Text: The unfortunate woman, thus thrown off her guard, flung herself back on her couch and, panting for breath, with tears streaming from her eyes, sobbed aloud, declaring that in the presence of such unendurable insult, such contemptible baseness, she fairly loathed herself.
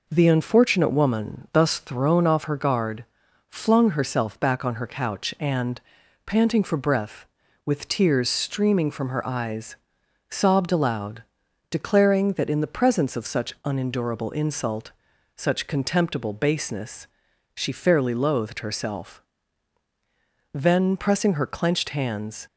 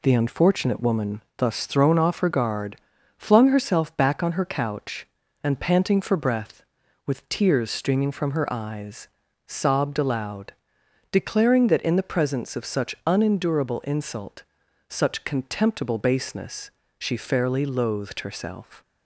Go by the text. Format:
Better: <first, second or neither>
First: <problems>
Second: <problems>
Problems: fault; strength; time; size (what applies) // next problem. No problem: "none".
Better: second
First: goes on to say "Then pressing her clenched hands"; strong; from 20.5 s on; 1.9 s long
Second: none